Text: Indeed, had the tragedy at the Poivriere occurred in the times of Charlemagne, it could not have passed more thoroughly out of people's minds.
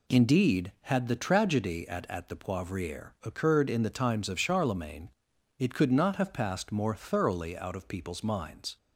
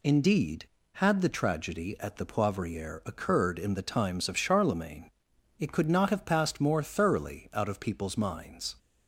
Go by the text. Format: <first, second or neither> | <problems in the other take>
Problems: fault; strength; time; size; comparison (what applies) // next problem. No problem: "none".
second | says "at" twice; at 2.0 s